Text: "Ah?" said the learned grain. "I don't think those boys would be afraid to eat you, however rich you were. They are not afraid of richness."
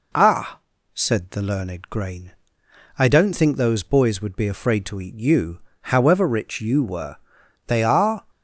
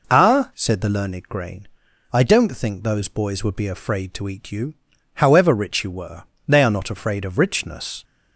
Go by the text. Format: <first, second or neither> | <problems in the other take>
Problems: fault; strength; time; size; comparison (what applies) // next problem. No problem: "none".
second | stops before "not afraid of richness"; at 8.2 s